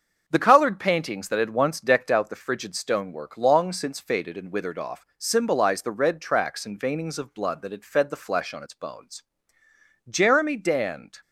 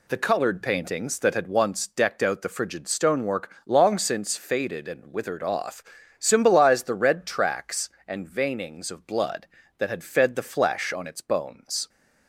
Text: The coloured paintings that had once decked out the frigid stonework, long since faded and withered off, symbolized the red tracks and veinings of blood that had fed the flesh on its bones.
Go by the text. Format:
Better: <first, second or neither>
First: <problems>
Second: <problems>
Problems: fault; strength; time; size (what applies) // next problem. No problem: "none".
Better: second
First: starts louder than the rest; until 1.2 s; 6.5 dB // goes on to say "Jeremy Dand"; noticeable; from 10.0 s on; 1.1 s long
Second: none